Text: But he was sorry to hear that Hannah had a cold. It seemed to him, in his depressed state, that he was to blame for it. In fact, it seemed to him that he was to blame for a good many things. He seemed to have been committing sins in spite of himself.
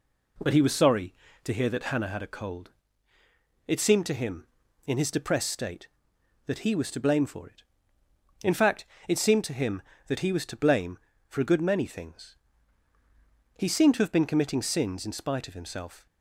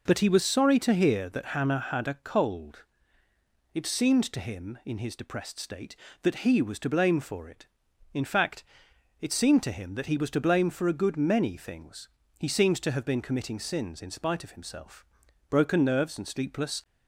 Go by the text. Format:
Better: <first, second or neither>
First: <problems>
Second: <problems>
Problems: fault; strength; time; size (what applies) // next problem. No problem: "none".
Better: first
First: none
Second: goes on to say "Broken nerves and sleepless"; from 15.4 s on; 1.3 s long